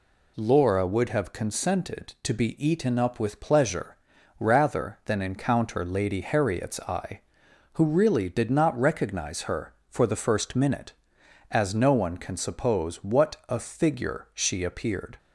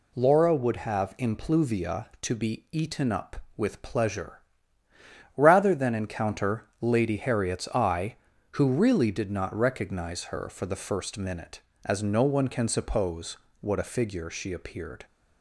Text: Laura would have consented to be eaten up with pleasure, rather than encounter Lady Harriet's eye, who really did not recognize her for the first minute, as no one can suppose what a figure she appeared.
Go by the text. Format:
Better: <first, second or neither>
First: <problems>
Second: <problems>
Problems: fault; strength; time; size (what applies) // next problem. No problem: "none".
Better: first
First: none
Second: says "impluvia" for "consented"; at 1.1 s // pauses between "suppose" and "what"; slight; at 13.3 s; 0.24 s long